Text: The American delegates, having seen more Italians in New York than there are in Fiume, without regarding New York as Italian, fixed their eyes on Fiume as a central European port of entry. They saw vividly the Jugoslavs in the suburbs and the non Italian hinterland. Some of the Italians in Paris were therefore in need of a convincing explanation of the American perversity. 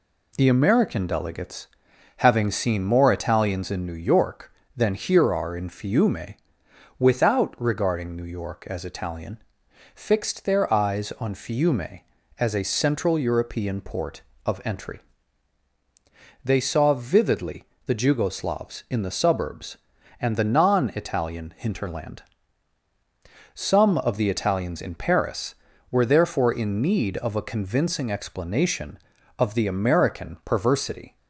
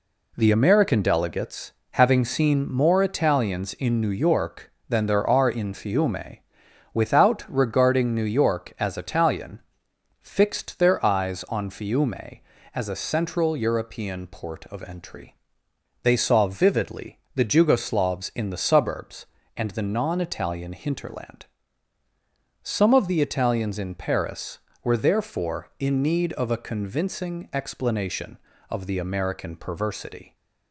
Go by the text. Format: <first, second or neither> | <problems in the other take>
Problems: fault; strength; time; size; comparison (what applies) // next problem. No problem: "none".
second | says "here" for "there"; at 4.9 s // pauses between "vividly" and "the"; slight; at 17.6 s; 0.22 s long; slight in the second